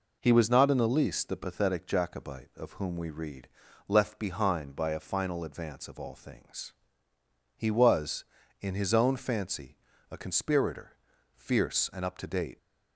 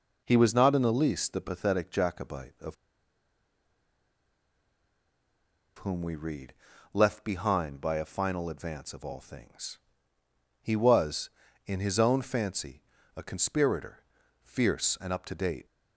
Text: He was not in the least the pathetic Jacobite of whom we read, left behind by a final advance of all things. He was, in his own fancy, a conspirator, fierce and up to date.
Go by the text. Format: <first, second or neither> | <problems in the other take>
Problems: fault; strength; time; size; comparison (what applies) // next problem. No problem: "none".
first | pauses between "of" and "whom"; strong; at 2.7 s; 3.0 s long